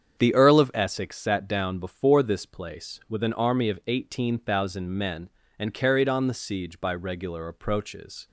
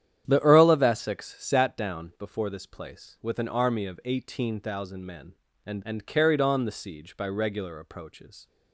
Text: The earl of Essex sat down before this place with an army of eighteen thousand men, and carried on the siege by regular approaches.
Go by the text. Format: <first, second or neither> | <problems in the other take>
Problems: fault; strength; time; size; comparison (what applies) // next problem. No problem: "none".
first | starts louder than the rest; strong; until 1.2 s; 10 dB; strong in the first // says "and" twice; at 5.8 s